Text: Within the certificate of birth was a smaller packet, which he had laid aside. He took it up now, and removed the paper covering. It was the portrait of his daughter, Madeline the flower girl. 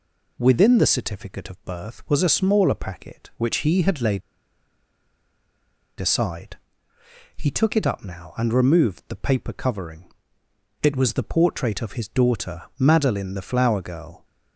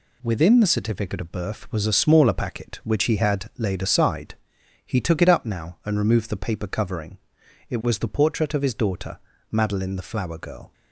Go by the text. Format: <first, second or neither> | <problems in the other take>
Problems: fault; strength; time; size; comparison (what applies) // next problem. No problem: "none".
second | pauses between "laid" and "aside"; strong; at 4.2 s; 1.8 s long